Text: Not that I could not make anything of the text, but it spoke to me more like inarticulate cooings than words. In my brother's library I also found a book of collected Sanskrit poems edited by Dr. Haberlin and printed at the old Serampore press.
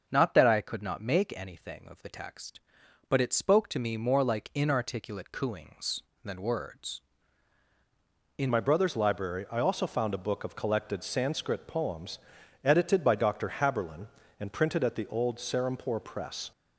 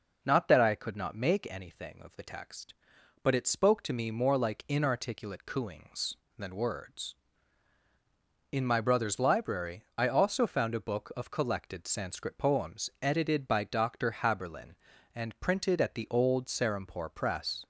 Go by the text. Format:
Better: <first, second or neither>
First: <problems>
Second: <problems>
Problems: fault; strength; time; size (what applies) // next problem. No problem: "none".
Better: second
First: starts louder than the rest; until 1.1 s; 6 dB // changes voice at "my"; from 8.5 s on; 8.0 s long // pauses between "poems" and "edited"; at 12.1 s; 0.44 s long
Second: none